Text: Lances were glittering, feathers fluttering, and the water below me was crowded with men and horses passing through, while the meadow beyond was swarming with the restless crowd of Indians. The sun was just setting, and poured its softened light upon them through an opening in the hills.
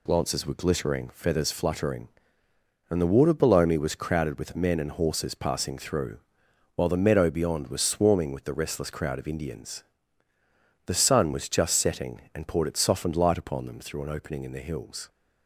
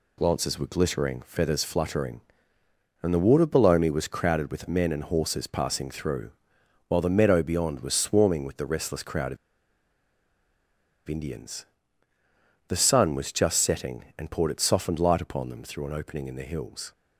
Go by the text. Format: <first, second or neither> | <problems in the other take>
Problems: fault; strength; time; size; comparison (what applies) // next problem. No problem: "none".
first | pauses between "of" and "Indians"; strong; at 9.3 s; 1.7 s long